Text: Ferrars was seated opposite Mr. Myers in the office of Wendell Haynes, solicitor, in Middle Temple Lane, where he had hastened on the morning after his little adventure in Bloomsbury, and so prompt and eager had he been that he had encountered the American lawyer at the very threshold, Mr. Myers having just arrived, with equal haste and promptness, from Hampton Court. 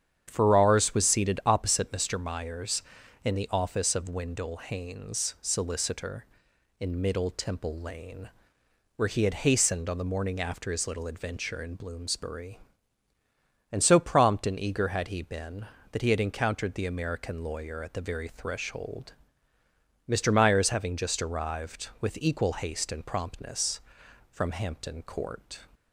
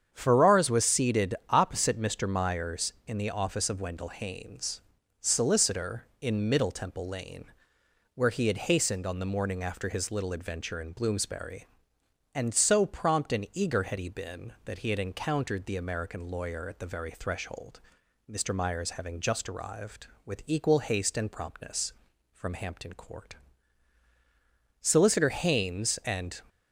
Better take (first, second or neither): first